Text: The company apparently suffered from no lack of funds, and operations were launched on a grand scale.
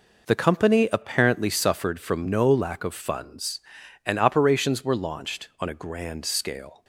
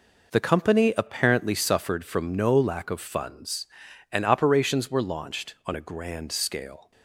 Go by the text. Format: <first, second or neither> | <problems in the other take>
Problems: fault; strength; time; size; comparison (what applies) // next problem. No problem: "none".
neither | none